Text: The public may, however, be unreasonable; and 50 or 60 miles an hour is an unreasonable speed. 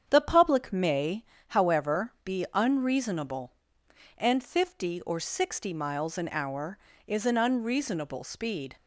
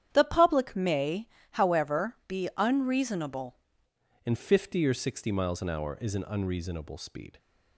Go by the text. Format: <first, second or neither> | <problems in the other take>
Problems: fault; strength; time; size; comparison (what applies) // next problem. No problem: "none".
first | starts louder than the rest; strong; until 1.1 s; 10 dB; strong in the first // changes voice at "and"; from 4.2 s on; 3.1 s long